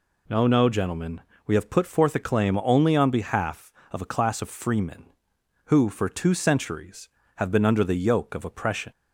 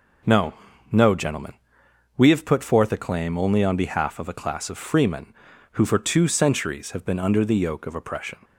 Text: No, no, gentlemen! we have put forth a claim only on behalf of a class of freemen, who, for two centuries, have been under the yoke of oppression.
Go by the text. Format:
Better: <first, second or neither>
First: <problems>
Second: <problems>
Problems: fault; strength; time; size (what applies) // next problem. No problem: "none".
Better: neither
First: none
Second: none